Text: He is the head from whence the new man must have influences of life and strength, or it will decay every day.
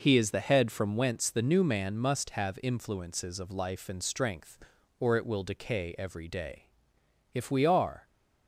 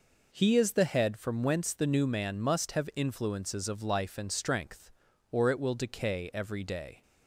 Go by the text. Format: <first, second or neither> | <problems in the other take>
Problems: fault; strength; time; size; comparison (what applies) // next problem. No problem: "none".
second | goes on to say "If we are"; noticeable; from 7.3 s on; 0.72 s long